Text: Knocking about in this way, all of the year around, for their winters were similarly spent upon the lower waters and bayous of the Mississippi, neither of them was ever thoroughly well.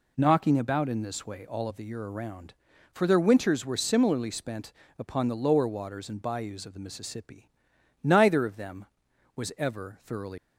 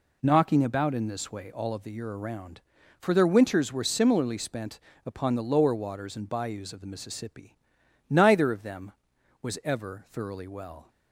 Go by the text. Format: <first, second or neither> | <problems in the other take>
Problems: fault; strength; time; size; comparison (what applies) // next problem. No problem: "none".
second | pauses between "spent" and "upon"; slight; at 4.7 s; 0.24 s long; slight in the second // stops before "well"; at 10.3 s